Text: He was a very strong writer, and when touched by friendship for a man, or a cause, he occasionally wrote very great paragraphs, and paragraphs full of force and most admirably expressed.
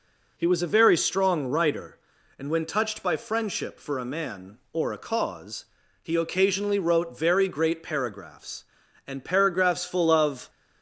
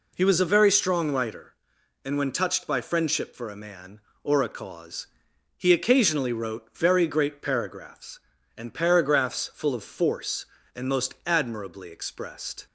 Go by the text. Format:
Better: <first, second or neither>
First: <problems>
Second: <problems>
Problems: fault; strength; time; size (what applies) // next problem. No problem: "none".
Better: second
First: stops before "force and most admirably expressed"; at 10.4 s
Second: none